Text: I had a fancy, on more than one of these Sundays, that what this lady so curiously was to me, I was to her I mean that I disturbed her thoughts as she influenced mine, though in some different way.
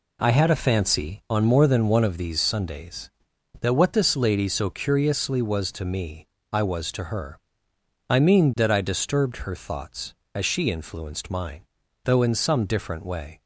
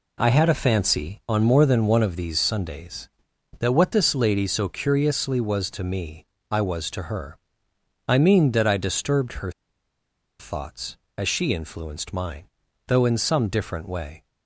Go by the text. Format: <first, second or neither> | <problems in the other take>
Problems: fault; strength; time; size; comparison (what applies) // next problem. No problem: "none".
first | pauses between "her" and "I"; noticeable; at 7.3 s; 0.68 s long; noticeable in the first // pauses between "her" and "thoughts"; noticeable; at 9.5 s; 0.88 s long